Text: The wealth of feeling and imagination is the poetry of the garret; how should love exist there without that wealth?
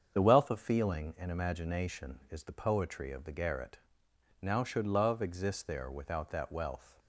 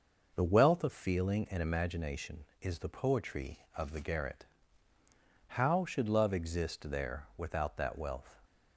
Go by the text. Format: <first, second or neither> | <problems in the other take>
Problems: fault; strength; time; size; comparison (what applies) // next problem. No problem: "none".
second | starts louder than the rest; strong; until 1.1 s; 7.5 dB // says "now" for "how"; at 4.4 s